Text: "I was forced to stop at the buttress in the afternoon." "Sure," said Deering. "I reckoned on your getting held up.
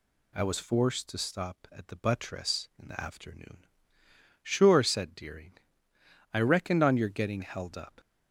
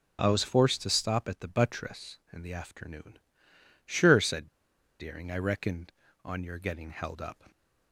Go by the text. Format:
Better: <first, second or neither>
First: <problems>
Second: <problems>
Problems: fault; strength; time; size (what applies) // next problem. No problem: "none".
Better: first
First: none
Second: pauses between "said" and "Deering"; noticeable; at 4.4 s; 0.51 s long